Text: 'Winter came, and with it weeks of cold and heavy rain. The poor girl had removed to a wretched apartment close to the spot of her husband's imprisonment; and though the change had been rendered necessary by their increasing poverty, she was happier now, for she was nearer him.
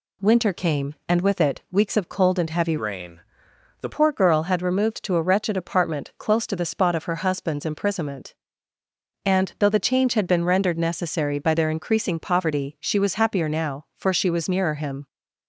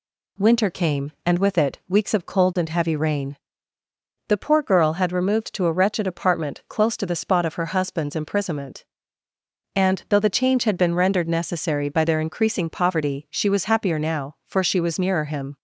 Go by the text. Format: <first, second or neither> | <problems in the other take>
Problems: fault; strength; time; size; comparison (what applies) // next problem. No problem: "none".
second | changes voice from "rain" to "The"; from 2.7 to 3.8 s; 1.1 s long